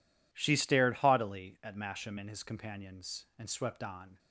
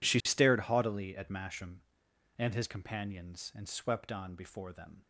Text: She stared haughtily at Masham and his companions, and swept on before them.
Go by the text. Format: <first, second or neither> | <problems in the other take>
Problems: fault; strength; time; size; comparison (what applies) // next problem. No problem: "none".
second | stops before "before them"; at 4.1 s